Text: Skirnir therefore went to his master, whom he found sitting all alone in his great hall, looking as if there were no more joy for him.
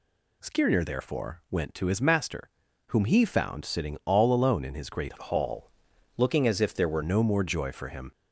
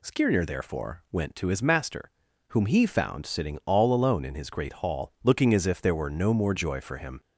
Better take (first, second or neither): second